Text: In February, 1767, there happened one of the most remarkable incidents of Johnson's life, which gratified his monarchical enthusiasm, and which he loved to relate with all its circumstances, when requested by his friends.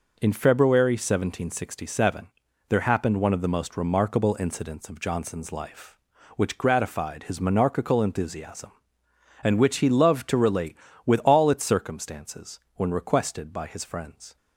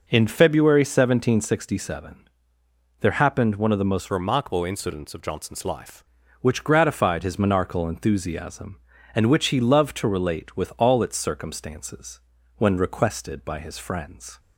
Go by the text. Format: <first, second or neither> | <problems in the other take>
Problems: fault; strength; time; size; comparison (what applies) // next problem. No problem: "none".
first | changes voice from "remarkable" to "life"; from 4.0 to 6.0 s; 2.0 s long